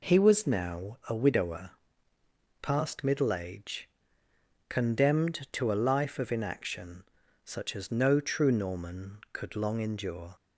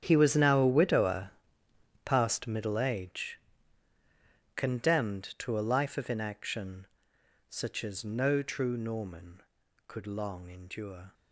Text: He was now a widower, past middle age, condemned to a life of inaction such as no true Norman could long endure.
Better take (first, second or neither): first